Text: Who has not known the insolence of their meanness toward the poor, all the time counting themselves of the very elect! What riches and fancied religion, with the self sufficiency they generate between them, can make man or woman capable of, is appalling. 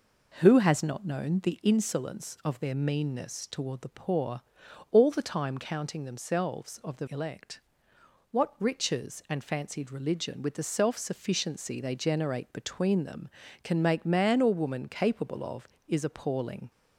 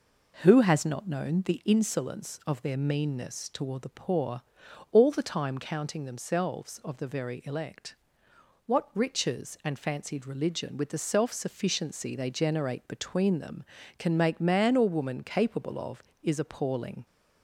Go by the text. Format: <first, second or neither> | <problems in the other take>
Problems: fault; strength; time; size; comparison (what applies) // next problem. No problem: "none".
second | skips "very"; at 7.0 s